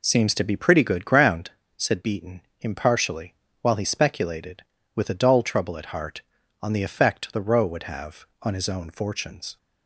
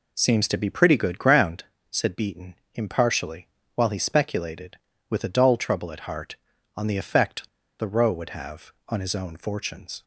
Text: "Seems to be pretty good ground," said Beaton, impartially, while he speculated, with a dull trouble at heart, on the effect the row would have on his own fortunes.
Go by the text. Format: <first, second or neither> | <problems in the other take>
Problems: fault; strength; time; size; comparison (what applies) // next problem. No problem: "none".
first | pauses between "effect" and "the"; slight; at 7.4 s; 0.30 s long